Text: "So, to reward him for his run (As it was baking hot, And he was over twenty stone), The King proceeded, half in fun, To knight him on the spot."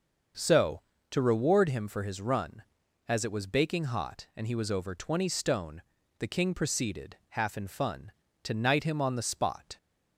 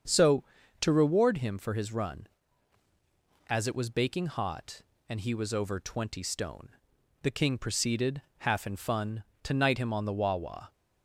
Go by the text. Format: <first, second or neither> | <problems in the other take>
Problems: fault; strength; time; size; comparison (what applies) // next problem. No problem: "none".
first | starts louder than the rest; until 1.4 s; 7 dB; also in the first // says "wawa" for "spot"; at 10.1 s